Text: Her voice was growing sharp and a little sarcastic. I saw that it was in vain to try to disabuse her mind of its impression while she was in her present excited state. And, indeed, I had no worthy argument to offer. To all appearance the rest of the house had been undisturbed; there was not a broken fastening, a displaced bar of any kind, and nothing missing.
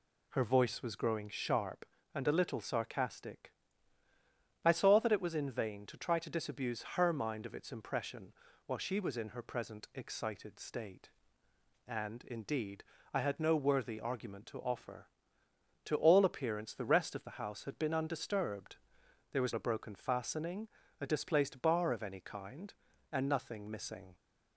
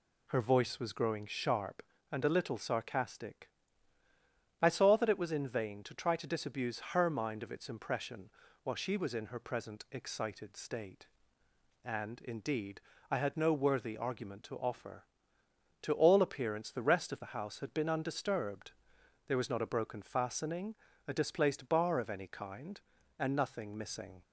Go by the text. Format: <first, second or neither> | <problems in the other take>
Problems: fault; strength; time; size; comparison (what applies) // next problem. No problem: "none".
second | pauses between "impression" and "while"; slight; at 8.3 s; 0.34 s long; slight in the second // skips "not"; at 19.5 s